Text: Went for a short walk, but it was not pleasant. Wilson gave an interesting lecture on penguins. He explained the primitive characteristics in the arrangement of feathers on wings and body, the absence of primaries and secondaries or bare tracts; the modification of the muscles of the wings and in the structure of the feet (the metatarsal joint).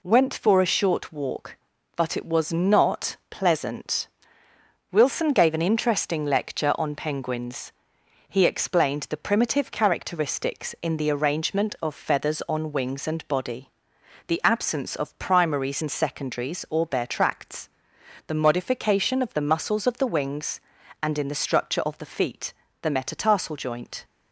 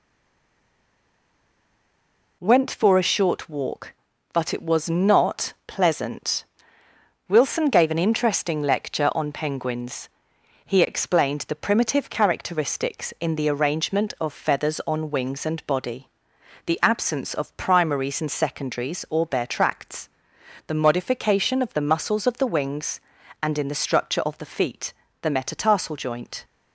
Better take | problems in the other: first | stays silent before the first word; until 2.4 s; 2.4 s long

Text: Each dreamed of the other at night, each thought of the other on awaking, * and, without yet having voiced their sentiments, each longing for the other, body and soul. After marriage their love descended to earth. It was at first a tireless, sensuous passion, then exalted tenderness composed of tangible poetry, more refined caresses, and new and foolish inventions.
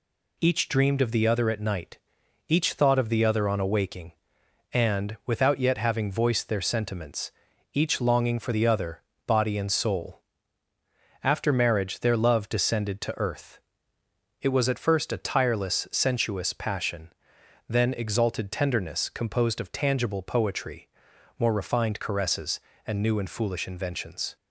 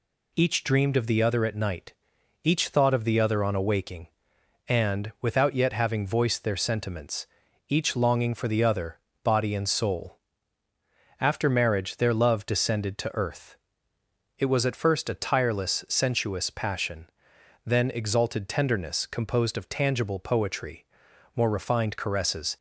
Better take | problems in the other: first | stops before "and new and foolish inventions"; at 22.5 s

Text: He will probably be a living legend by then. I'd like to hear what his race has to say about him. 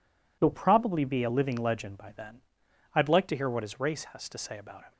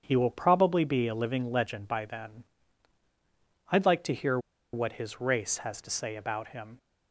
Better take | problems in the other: first | starts louder than the rest; strong; until 1.0 s; 7.5 dB // pauses between "hear" and "what"; slight; at 4.3 s; 0.35 s long

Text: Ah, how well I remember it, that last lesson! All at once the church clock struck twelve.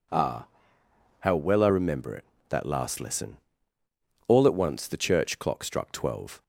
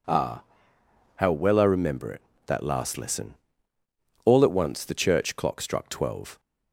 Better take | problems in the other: neither | none

